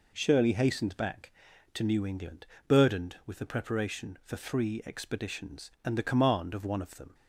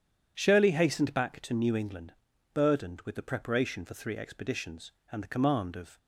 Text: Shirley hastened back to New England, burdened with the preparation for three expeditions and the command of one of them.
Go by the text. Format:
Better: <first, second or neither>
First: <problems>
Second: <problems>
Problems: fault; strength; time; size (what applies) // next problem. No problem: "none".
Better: first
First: none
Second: stops before "one of them"; at 5.9 s